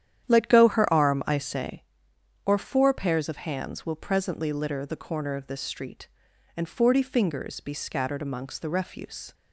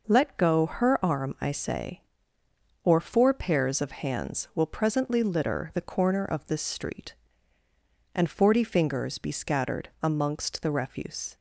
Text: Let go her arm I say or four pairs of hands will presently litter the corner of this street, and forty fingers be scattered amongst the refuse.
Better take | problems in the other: second | starts louder than the rest; strong; until 1.9 s; 10 dB

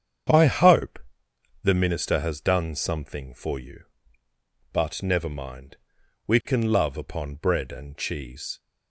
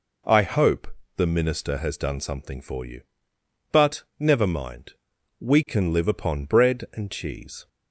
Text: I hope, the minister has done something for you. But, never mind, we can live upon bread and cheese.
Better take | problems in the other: second | starts louder than the rest; strong; until 1.9 s; 8.5 dB // says "love" for "live"; at 6.7 s

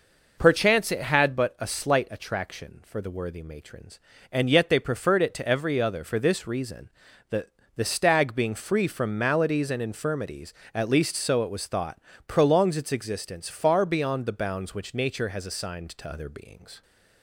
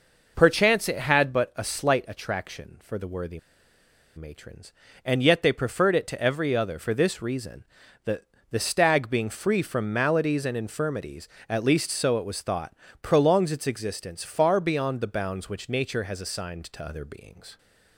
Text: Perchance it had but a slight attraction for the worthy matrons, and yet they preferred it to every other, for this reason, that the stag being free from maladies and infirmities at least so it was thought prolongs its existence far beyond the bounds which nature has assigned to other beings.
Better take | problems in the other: first | pauses between "worthy" and "matrons"; noticeable; at 3.3 s; 0.76 s long // pauses between "that" and "the"; slight; at 8.2 s; 0.26 s long; slight in the first // pauses between "thought" and "prolongs"; slight; at 12.7 s; 0.28 s long; slight in the first

